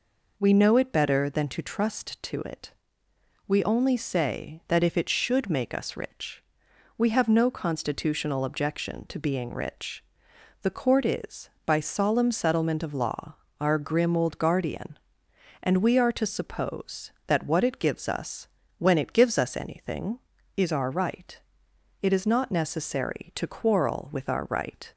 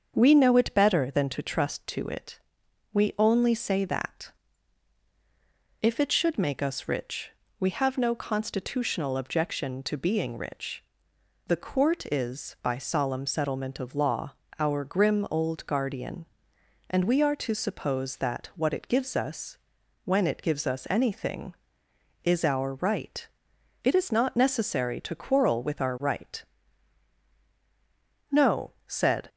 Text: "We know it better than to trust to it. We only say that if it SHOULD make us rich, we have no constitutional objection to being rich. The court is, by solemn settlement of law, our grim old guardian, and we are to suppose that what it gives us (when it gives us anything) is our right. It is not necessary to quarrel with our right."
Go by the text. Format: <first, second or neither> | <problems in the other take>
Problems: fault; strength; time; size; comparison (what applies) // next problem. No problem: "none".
first | starts louder than the rest; until 1.1 s; 7 dB // pauses between "that" and "if"; strong; at 4.3 s; 1.5 s long // goes on to say "No said"; noticeable; from 28.3 s on; 0.98 s long